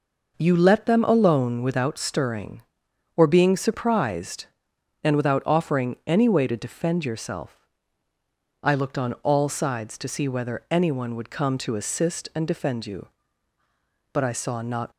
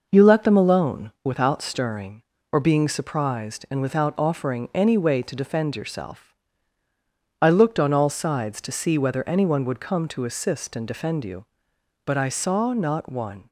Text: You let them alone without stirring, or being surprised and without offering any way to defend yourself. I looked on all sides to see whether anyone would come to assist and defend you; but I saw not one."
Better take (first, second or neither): second